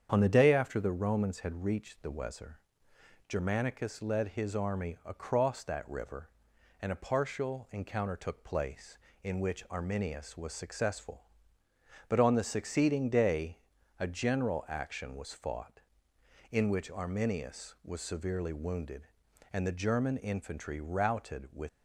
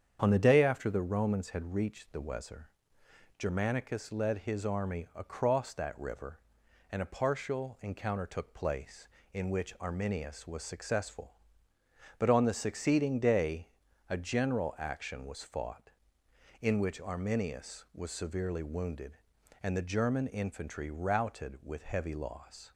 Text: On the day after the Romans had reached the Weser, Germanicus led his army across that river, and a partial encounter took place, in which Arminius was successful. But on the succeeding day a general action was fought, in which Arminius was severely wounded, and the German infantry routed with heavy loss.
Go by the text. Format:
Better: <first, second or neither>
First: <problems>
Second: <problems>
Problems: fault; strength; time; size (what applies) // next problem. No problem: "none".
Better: second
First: starts louder than the rest; strong; until 1.1 s; 8 dB // pauses between "day" and "a"; at 13.5 s; 0.42 s long // stops before "heavy loss"; at 21.6 s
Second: starts louder than the rest; strong; until 1.2 s; 8 dB // pauses between "day" and "a"; at 13.6 s; 0.42 s long